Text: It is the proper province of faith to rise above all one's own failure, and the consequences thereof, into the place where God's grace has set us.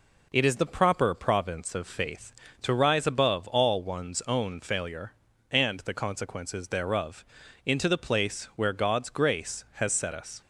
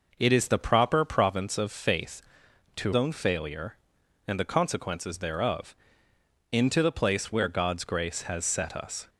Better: first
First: none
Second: skips "rise above all one's"; at 2.9 s

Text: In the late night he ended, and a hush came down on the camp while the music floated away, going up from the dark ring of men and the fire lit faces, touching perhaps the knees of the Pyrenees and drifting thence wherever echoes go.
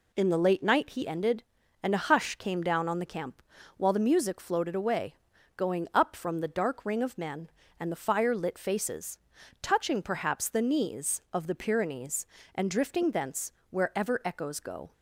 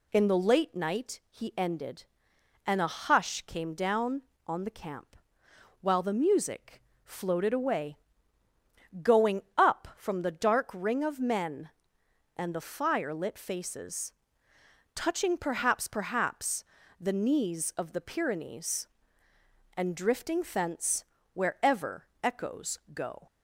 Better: first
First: pauses between "camp" and "while"; slight; at 3.4 s; 0.36 s long // pauses between "thence" and "wherever"; slight; at 13.5 s; 0.18 s long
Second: pauses between "camp" and "while"; noticeable; at 5.1 s; 0.66 s long // pauses between "music" and "floated"; slight; at 6.8 s; 0.24 s long // says "perhaps" twice; at 15.8 s // pauses between "thence" and "wherever"; slight; at 21.0 s; 0.30 s long // pauses between "wherever" and "echoes"; slight; at 22.0 s; 0.16 s long // pauses between "echoes" and "go"; slight; at 22.7 s; 0.16 s long

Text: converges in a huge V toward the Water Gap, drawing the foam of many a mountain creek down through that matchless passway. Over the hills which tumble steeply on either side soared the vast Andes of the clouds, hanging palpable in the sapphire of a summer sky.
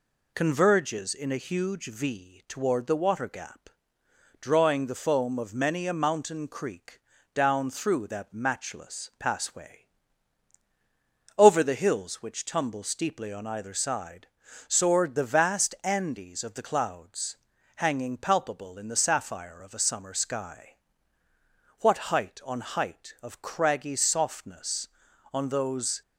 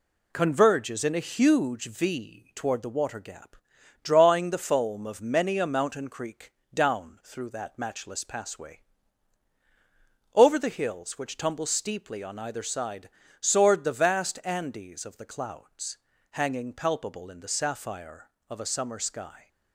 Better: second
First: pauses between "creek" and "down"; slight; at 6.9 s; 0.34 s long // pauses between "side" and "soared"; at 14.2 s; 0.40 s long // goes on to say "What height on height of craggy softness on those"; strong; from 21.7 s on; 4.2 s long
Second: pauses between "creek" and "down"; slight; at 6.5 s; 0.20 s long // pauses between "side" and "soared"; slight; at 13.0 s; 0.30 s long

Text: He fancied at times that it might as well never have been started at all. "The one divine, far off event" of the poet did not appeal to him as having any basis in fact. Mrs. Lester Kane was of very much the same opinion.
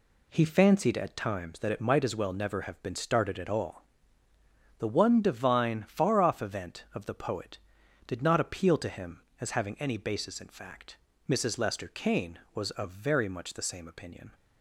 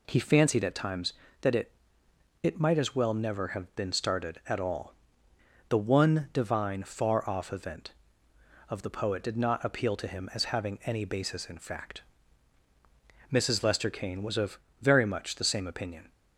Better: first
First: none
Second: says "it" twice; at 2.4 s // pauses between "of" and "very"; slight; at 14.5 s; 0.20 s long

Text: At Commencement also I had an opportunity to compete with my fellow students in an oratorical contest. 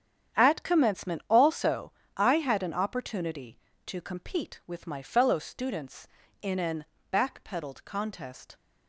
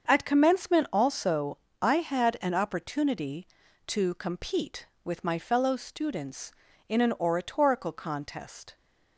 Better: second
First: starts louder than the rest; strong; until 1.4 s; 9 dB // pauses between "also" and "I"; slight; at 1.9 s; 0.24 s long // says "backpedaled" for "oratorical"; at 7.1 s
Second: starts louder than the rest; until 1.1 s; 7 dB // pauses between "also" and "I"; slight; at 1.5 s; 0.24 s long

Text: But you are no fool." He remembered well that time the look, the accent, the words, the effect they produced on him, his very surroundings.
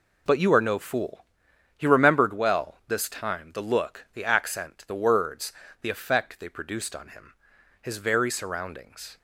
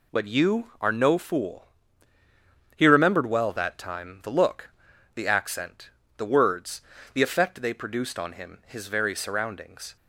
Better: second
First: says "this" for "that"; at 2.8 s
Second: none

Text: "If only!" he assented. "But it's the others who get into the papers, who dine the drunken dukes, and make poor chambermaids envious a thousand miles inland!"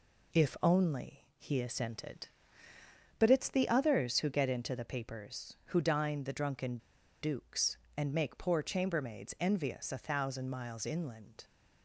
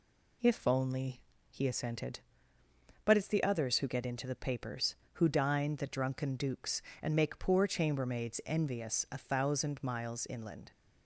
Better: second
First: pauses between "drunken" and "dukes"; at 6.7 s; 0.44 s long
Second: none

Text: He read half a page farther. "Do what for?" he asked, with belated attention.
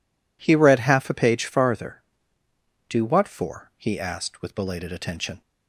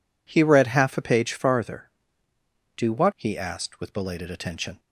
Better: first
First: none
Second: skips "for"; at 3.1 s

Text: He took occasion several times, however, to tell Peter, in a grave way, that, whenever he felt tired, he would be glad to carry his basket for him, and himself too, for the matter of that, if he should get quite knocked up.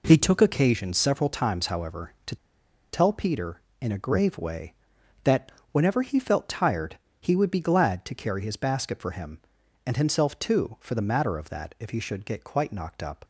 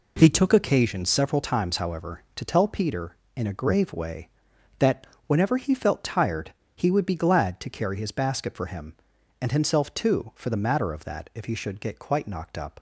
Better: second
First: pauses between "to" and "tell"; noticeable; at 2.3 s; 0.57 s long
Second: none

